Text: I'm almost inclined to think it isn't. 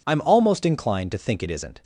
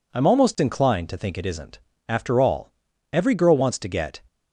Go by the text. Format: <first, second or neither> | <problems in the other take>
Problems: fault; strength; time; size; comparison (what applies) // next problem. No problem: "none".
first | goes on to say "After all every girl wants to get"; strong; from 2.0 s on; 2.1 s long